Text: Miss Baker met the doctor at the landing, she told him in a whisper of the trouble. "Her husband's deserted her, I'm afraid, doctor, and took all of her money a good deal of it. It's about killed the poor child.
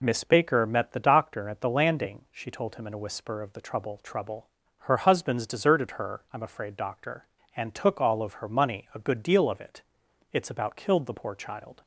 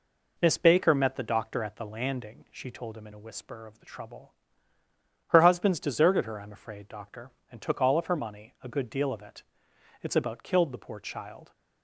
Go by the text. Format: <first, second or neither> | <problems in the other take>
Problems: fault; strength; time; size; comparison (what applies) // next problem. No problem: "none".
second | says "trouble" twice; at 3.9 s